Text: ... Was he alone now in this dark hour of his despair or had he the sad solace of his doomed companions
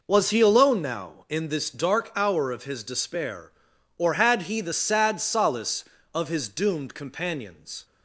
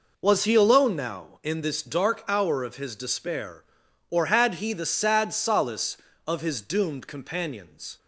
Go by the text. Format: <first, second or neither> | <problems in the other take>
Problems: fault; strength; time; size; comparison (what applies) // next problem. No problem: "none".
neither | none